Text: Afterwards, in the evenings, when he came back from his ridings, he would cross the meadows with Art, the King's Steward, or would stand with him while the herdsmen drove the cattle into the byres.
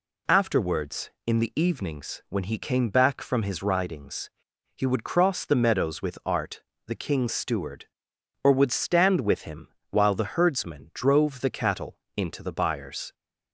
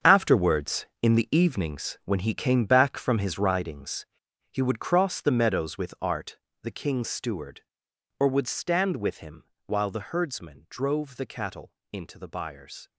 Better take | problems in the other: first | gets quieter; strong; throughout; 12 dB // pauses between "him" and "while"; slight; at 9.4 s; 0.24 s long; slight in the first // pauses between "cattle" and "into"; slight; at 11.7 s; 0.16 s long; slight in the first

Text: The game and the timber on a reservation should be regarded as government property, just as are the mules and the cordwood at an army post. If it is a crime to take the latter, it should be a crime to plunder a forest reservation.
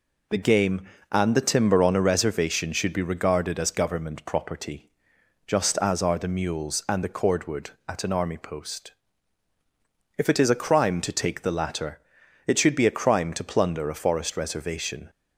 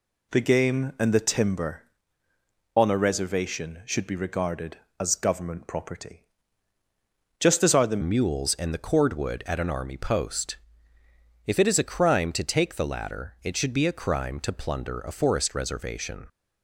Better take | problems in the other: first | changes voice at "mules"; from 8.0 s on; 8.2 s long

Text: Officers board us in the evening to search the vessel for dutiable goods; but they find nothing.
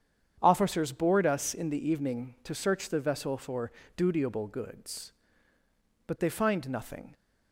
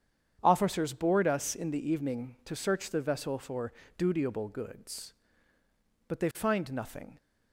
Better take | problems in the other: neither | starts louder than the rest; strong; the same in both // pauses between "for" and "dutiable"; slight; the same in both

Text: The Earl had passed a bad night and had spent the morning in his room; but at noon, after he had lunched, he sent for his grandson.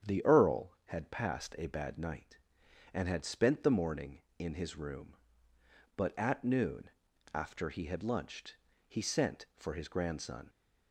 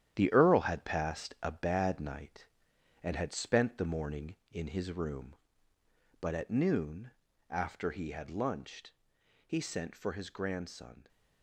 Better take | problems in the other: first | gets quieter; strong; throughout; 8.5 dB // starts louder than the rest; strong; until 1.1 s; 10.5 dB; strong in the first

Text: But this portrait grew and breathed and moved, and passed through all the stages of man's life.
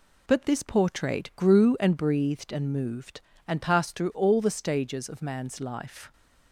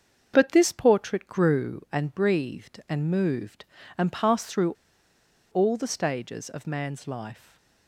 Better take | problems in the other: first | starts louder than the rest; until 1.3 s; 6.5 dB // pauses between "through" and "all"; noticeable; at 4.7 s; 0.78 s long // stays silent after the last word; slight; from 7.3 s on; 0.5 s long

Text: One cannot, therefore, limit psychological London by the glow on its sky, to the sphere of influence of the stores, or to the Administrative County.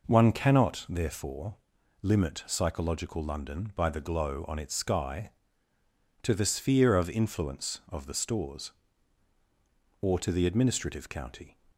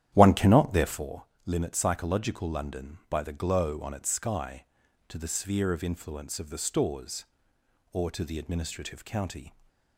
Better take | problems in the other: first | starts louder than the rest; strong; until 1.2 s; 11 dB

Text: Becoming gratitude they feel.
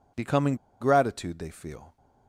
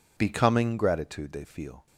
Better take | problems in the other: second | pauses between "Becoming" and "gratitude"; slight; at 0.5 s; 0.25 s long

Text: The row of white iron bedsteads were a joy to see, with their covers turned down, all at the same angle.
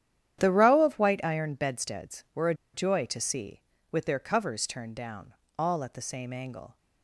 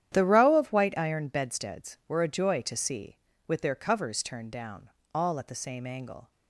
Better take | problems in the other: second | starts louder than the rest; strong; until 1.4 s; 10.5 dB; strong in the second // pauses between "a" and "joy"; slight; at 2.5 s; 0.20 s long

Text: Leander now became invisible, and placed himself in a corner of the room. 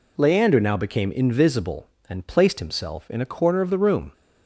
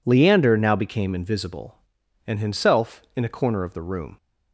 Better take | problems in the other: first | skips "placed"; at 2.4 s

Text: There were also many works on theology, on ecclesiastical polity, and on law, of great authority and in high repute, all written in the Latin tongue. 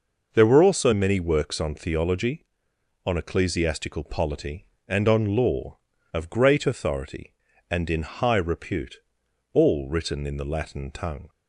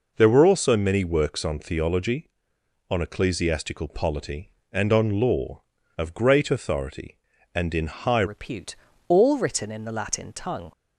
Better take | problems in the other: first | changes voice at "repute"; from 8.2 s on; 2.5 s long

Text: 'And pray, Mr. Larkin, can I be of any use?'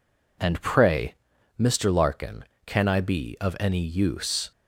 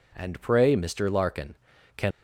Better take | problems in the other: first | stops before "I be of any use"; at 2.1 s

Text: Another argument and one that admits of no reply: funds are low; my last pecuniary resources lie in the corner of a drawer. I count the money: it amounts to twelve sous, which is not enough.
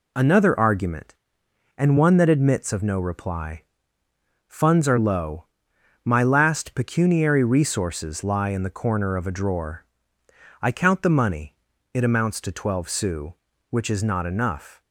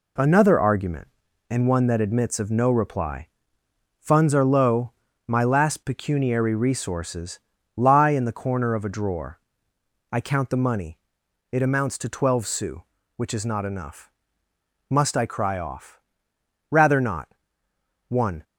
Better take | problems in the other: first | pauses between "resources" and "lie"; at 7.3 s; 0.38 s long // goes on to say "Must I cry off Rather not One"; strong; from 14.8 s on; 3.5 s long

